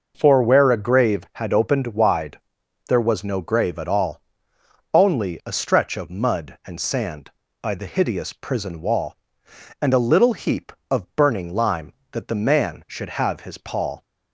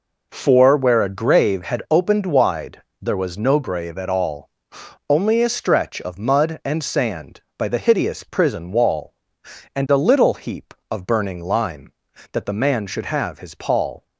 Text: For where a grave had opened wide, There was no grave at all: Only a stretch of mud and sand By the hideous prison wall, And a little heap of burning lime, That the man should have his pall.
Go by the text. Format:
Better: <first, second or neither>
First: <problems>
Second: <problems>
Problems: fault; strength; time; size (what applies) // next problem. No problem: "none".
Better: neither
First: none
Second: none